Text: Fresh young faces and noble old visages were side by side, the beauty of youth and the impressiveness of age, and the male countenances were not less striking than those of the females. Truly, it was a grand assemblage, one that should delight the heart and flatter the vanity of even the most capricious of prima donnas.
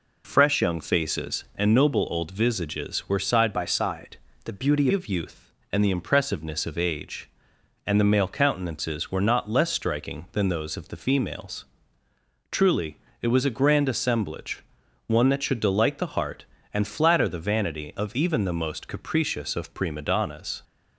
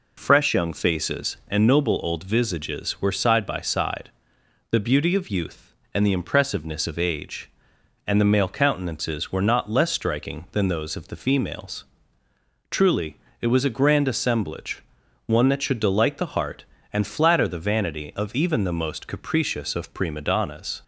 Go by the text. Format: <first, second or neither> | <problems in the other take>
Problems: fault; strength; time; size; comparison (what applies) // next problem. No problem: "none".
second | changes voice from "by" to "beauty"; from 3.5 to 4.8 s; 1.3 s long